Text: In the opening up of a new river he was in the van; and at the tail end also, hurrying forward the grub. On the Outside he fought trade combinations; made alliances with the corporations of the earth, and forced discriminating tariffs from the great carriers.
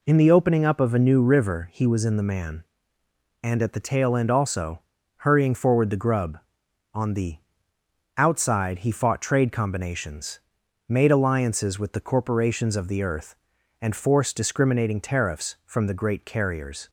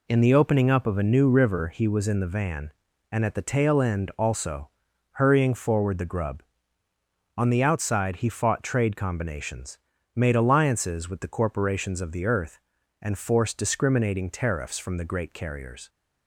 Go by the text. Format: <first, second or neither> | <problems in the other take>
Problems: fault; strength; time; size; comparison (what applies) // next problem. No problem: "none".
second | says "man" for "van"; at 2.2 s // pauses between "the" and "Outside"; noticeable; at 7.3 s; 0.80 s long